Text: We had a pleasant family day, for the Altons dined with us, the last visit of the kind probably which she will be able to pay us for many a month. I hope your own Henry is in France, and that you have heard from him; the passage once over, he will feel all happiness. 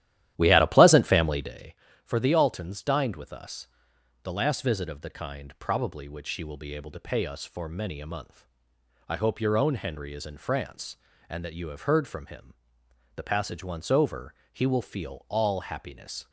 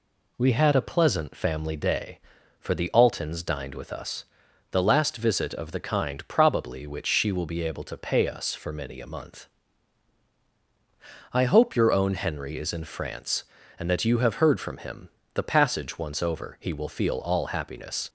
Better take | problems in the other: second | starts louder than the rest; strong; until 1.7 s; 12.5 dB

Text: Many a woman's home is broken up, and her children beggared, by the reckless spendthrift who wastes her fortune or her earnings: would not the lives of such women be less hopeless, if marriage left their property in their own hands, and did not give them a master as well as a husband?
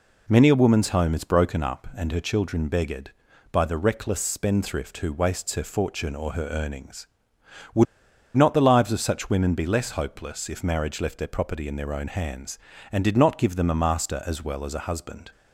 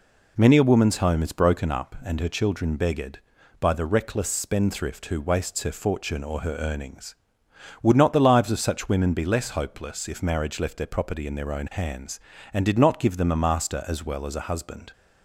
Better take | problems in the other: second | pauses between "would" and "not"; noticeable; at 7.8 s; 0.51 s long

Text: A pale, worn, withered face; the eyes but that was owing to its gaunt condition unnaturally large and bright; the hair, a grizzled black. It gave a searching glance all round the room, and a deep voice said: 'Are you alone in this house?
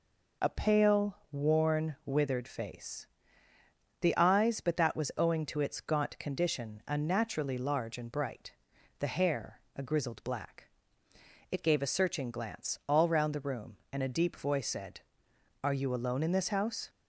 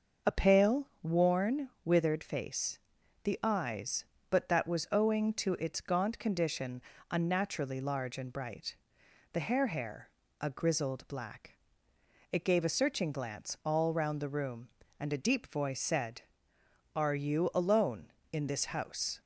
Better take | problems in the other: first | starts louder than the rest; noticeable; until 1.4 s; 6 dB // pauses between "condition" and "unnaturally"; slight; at 6.8 s; 0.28 s long // says "hair" twice; at 9.6 s

